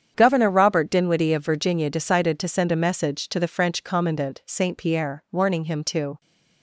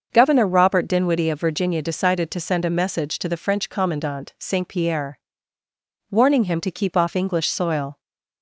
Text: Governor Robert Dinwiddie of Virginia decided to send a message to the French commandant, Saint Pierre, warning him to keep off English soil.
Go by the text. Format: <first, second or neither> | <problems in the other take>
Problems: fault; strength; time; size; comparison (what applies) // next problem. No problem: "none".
second | starts louder than the rest; strong; until 1.1 s; 8.5 dB; also in the second // stops before "keep off English soil"; at 6.2 s